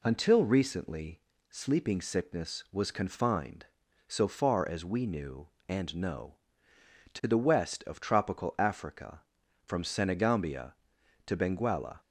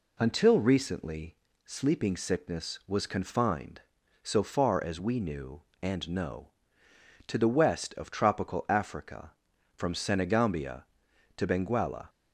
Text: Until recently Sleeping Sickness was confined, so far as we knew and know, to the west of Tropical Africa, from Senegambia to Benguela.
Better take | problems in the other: neither | pauses between "recently" and "Sleeping"; slight; the same in both

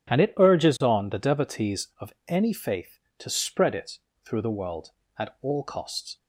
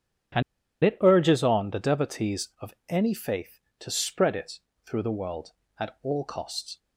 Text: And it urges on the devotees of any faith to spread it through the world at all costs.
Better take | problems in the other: first | pauses between "And" and "it"; at 0.4 s; 0.43 s long // pauses between "of" and "any"; slight; at 2.7 s; 0.16 s long; slight in the first // pauses between "it" and "through"; slight; at 4.5 s; 0.28 s long; slight in the first

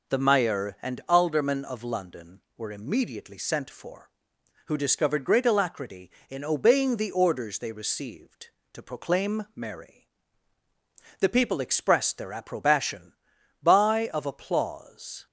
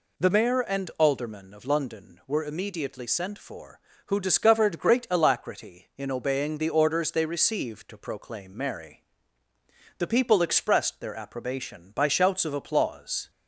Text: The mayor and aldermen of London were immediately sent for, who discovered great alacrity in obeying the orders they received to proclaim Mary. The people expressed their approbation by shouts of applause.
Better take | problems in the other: second | skips "shouts"; at 14.1 s

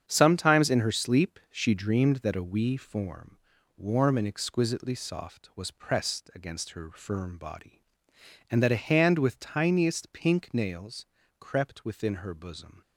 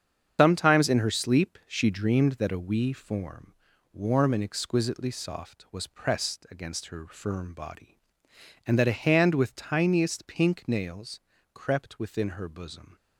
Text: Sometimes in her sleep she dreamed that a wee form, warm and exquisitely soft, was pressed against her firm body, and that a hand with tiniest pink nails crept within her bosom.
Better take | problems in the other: first | loses the start of "Sometimes"; at 0.3 s; 120 ms // starts louder than the rest; strong; until 1.3 s; 8 dB; strong in the first // pauses between "nails" and "crept"; slight; at 11.1 s; 0.34 s long; slight in the first

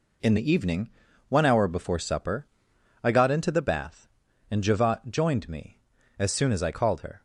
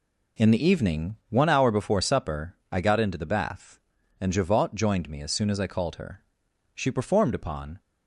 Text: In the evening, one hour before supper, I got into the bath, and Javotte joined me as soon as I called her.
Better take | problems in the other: first | goes on to say "She performed upon"; noticeable; from 6.7 s on; 1.0 s long

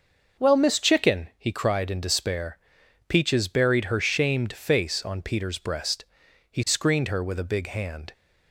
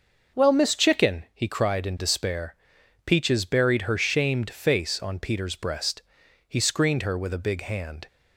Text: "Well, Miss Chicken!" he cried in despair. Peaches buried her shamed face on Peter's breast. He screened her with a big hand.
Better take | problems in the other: neither | starts louder than the rest; noticeable; the same in both

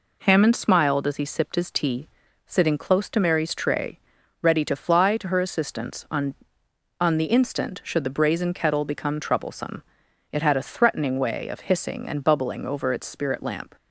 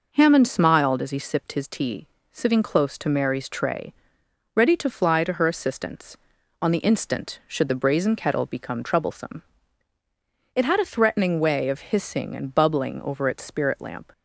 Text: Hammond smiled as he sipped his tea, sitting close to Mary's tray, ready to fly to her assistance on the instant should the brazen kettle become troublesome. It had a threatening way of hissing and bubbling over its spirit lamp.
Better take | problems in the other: second | says "on" twice; at 6.9 s

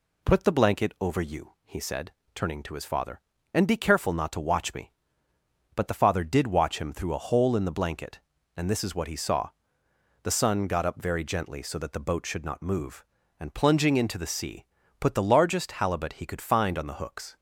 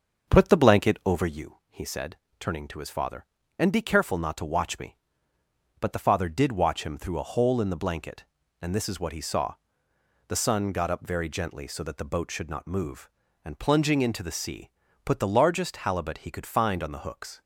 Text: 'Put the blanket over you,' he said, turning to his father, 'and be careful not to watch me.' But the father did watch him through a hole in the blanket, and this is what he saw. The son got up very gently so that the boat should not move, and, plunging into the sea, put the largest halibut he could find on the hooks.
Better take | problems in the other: first | starts louder than the rest; until 1.4 s; 6.5 dB

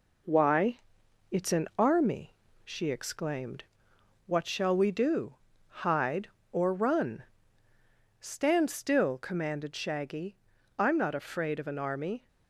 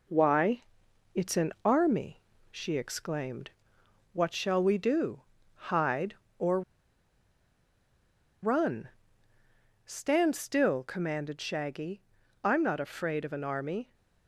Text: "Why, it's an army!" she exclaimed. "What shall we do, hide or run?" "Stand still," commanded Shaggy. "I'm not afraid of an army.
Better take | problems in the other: first | pauses between "or" and "run"; strong; at 6.6 s; 1.8 s long

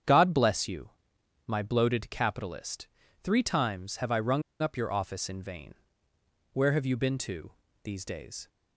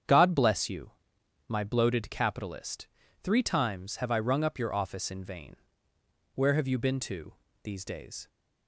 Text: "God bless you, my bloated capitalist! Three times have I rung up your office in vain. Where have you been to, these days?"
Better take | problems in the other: second | starts louder than the rest; strong; until 1.6 s; 8 dB; strong in the second // pauses between "rung" and "up"; slight; at 4.4 s; 0.19 s long

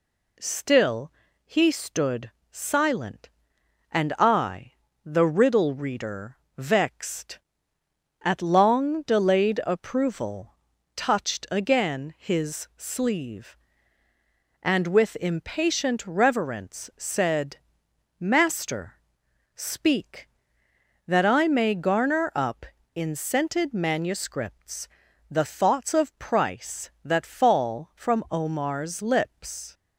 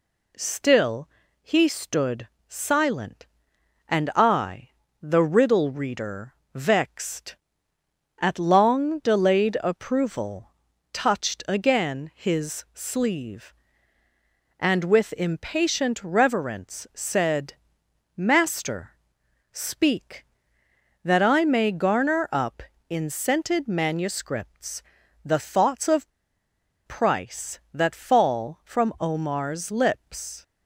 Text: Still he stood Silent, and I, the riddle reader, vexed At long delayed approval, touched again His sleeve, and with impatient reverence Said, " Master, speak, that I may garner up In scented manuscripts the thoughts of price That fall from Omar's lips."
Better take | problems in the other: first | pauses between "Still" and "he"; slight; at 1.0 s; 0.34 s long; slight in the first // pauses between "stood" and "Silent"; slight; at 2.2 s; 0.24 s long; slight in the first // pauses between "manuscripts" and "the"; at 24.8 s; 0.42 s long; also in the first // pauses between "of" and "price"; noticeable; at 26.1 s; 0.75 s long

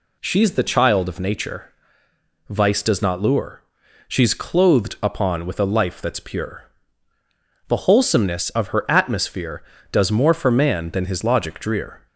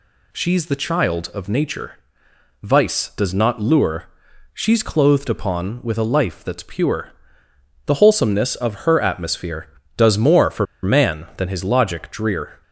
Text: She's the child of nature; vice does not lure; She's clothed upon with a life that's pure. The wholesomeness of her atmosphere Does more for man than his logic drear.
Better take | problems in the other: first | pauses between "for" and "man"; slight; at 10.6 s; 0.18 s long

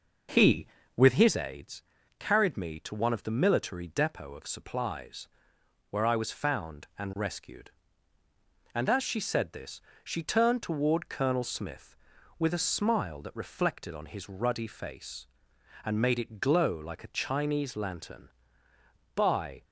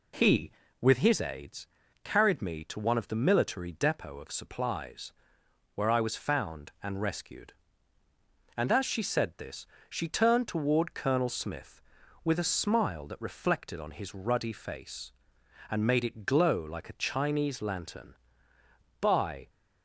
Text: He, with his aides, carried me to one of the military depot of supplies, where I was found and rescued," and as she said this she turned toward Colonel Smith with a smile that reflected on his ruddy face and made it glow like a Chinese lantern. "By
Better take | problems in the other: second | starts louder than the rest; noticeable; until 1.5 s; 5.5 dB // pauses between "this" and "she"; slight; at 9.8 s; 0.20 s long; slight in the second

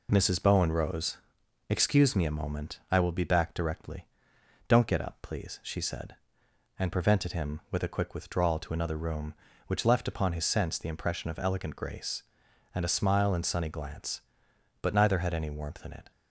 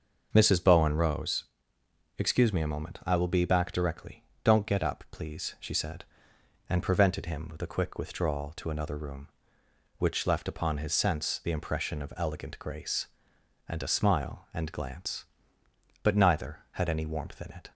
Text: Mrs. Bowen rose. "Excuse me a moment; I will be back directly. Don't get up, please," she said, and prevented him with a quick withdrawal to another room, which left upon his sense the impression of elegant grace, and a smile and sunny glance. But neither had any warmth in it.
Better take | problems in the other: first | starts louder than the rest; noticeable; until 1.3 s; 6 dB // skips "sunny"; at 14.7 s

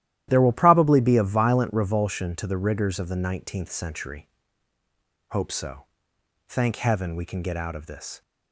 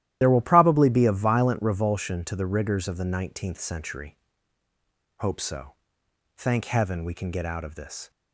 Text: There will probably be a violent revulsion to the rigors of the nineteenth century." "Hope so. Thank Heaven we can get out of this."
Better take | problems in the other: first | loses the start of "There"; at 0.2 s; 40 ms // starts louder than the rest; strong; until 1.2 s; 13 dB; strong in the first

